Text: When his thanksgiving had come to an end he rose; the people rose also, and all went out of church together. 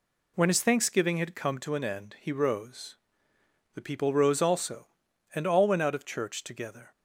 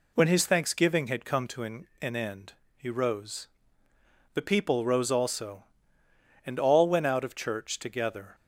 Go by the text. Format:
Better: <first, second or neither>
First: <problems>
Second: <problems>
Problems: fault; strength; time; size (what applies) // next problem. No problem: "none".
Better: first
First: none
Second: says "an" twice; at 2.0 s // pauses between "end" and "he"; slight; at 2.5 s; 0.24 s long